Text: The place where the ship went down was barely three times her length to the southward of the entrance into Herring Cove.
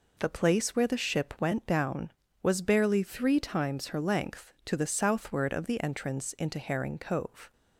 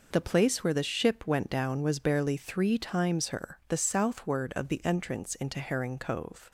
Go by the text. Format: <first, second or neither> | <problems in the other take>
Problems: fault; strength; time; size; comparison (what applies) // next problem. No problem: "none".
first | skips "length to"; at 3.6 s